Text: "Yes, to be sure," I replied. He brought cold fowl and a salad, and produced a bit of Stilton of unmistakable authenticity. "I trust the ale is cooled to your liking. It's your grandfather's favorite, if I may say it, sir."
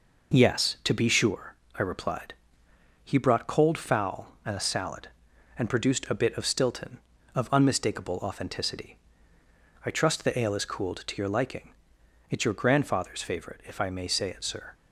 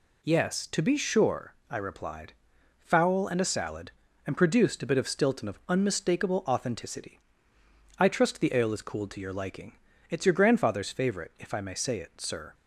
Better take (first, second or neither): first